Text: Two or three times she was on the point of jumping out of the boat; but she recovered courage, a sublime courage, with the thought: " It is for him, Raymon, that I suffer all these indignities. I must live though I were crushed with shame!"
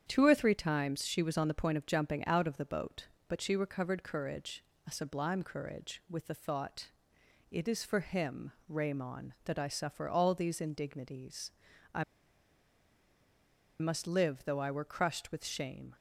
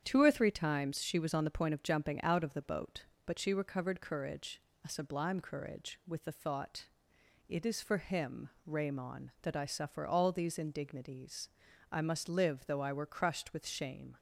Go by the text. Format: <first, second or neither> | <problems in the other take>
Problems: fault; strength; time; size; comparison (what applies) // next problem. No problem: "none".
second | starts louder than the rest; strong; until 1.0 s; 8.5 dB; strong in the second // pauses between "I" and "must"; strong; at 12.0 s; 1.7 s long